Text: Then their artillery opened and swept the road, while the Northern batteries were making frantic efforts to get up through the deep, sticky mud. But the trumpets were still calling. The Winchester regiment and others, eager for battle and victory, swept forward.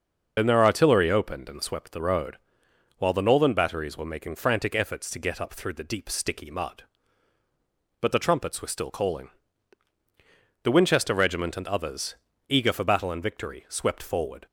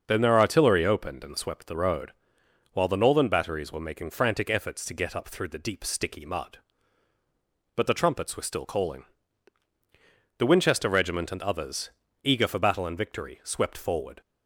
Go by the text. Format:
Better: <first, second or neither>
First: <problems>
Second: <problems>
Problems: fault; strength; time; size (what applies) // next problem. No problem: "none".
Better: second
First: loses the start of "Then"; at 0.3 s; 55 ms // starts louder than the rest; noticeable; until 1.3 s; 6 dB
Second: starts louder than the rest; until 1.0 s; 6.5 dB